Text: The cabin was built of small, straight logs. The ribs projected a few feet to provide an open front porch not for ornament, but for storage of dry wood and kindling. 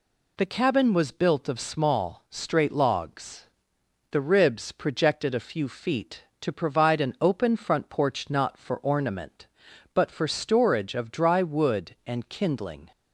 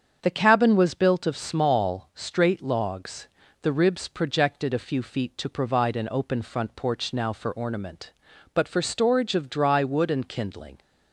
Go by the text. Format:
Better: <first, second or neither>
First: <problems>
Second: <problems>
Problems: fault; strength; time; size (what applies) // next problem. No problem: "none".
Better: first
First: none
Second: starts louder than the rest; strong; until 1.2 s; 7.5 dB // says "now" for "not"; at 7.1 s